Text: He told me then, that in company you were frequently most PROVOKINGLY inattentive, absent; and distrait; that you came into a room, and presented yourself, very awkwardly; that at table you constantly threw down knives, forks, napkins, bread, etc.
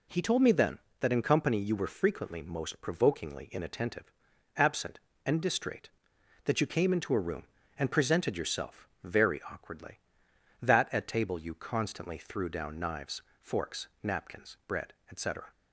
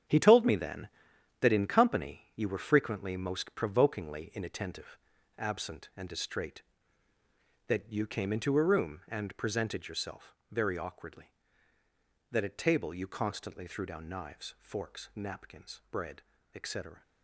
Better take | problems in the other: first | gets quieter; strong; throughout; 8.5 dB

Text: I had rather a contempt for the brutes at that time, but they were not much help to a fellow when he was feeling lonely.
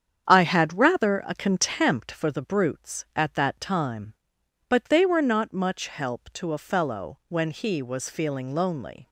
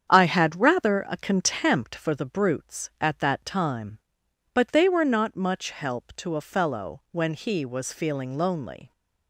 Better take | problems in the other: neither | starts louder than the rest; strong; the same in both

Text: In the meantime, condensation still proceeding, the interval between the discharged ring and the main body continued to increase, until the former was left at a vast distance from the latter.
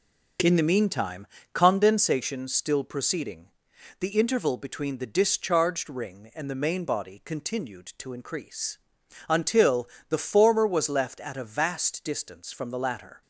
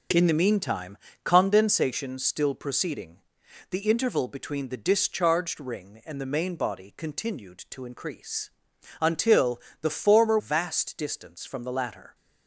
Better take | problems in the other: first | pauses between "until" and "the"; slight; at 9.6 s; 0.18 s long; slight in the first // skips "was left at a"; at 10.3 s

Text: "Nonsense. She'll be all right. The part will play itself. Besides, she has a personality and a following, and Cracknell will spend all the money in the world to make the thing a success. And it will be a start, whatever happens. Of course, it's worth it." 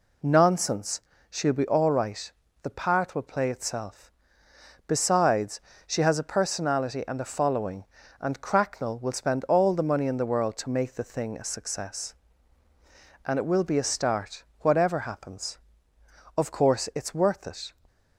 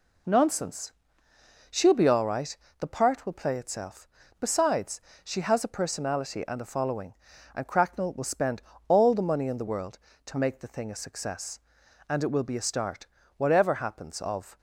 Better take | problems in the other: first | pauses between "spend" and "all"; slight; at 8.6 s; 0.26 s long // stops before "course it's worth it"; at 14.5 s

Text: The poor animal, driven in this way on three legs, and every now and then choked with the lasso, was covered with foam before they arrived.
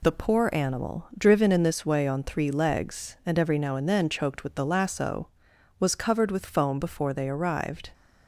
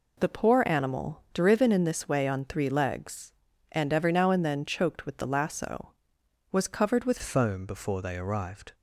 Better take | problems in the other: first | changes voice at "foam"; from 7.2 s on; 1.5 s long

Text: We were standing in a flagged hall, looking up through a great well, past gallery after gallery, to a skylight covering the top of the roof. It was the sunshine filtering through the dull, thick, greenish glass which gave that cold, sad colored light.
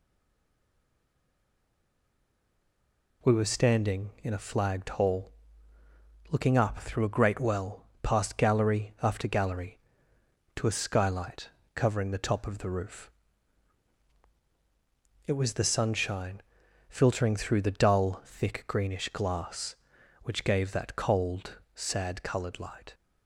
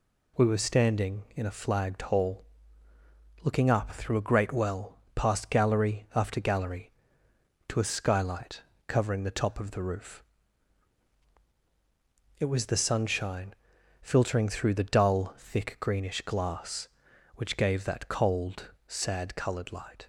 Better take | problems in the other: second | stays silent before the first word; strong; until 3.2 s; 3.2 s long // pauses between "skylight" and "covering"; slight; at 11.4 s; 0.26 s long; slight in the second // pauses between "sunshine" and "filtering"; noticeable; at 16.4 s; 0.46 s long; noticeable in the second

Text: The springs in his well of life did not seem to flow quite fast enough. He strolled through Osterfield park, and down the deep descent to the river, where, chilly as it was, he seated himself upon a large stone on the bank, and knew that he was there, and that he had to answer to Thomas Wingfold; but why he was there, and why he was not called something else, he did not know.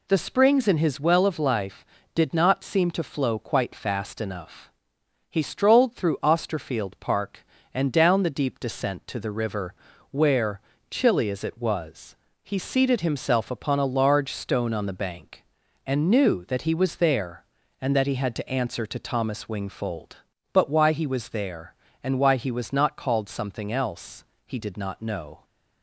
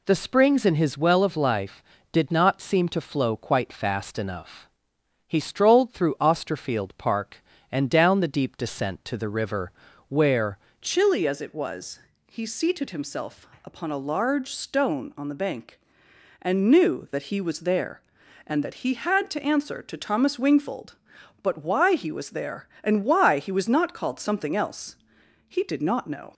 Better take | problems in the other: first | changes voice at "chilly"; from 10.8 s on; 15.5 s long // pauses between "himself" and "upon"; slight; at 13.4 s; 0.16 s long

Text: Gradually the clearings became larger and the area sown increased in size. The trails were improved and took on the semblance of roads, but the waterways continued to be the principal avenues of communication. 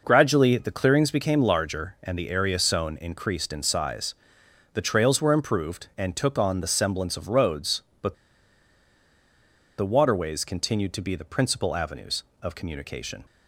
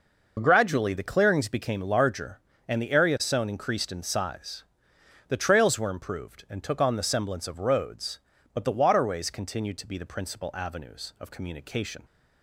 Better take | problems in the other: second | pauses between "but" and "the"; strong; at 8.1 s; 1.6 s long

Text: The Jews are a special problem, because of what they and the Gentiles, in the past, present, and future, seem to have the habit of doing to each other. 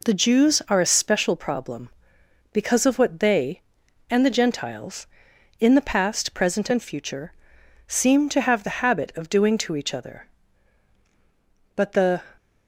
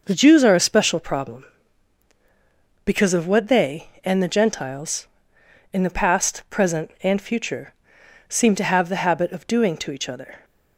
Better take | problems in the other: second | goes on to say "But the"; slight; from 11.7 s on; 0.46 s long

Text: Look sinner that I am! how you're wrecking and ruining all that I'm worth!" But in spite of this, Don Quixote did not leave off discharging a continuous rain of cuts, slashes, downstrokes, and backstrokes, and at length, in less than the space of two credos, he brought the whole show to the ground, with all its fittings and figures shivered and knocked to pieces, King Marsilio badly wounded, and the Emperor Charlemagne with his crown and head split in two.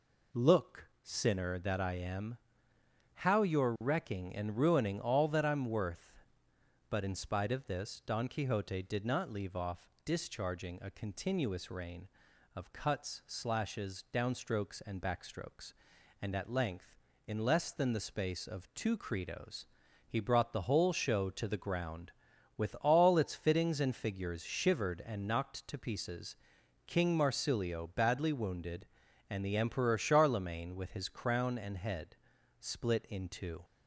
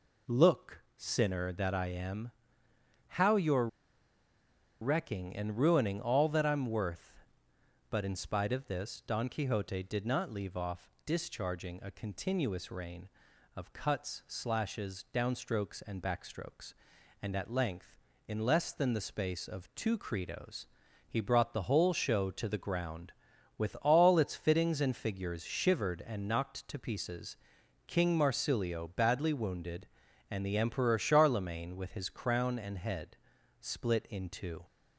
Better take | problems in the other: first | pauses between "Look" and "sinner"; slight; at 0.7 s; 0.16 s long; slight in the first // pauses between "you're" and "wrecking"; at 3.6 s; 1.1 s long // pauses between "off" and "discharging"; slight; at 10.8 s; 0.16 s long; slight in the first // pauses between "head" and "split"; noticeable; at 33.1 s; 0.46 s long; noticeable in the first

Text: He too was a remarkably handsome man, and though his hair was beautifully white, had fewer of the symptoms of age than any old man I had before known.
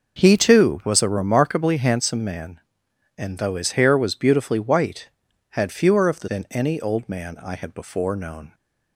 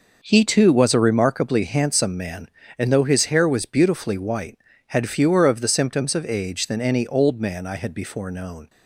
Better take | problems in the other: second | skips "symptoms of age"; at 6.2 s

